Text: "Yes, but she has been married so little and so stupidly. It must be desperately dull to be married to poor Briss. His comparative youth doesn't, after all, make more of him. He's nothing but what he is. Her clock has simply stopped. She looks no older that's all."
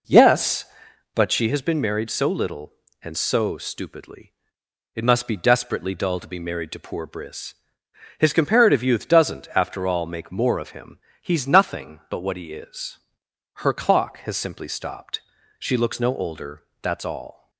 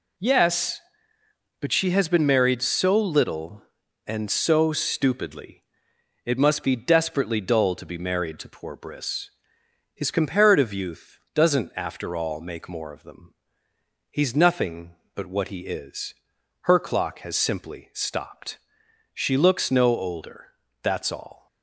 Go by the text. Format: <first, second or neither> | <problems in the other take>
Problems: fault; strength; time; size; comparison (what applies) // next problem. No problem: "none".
first | pauses between "youth" and "doesn't"; slight; at 11.1 s; 0.16 s long // says "them" for "him"; at 13.0 s // pauses between "older" and "that's"; slight; at 20.5 s; 0.30 s long; slight in the first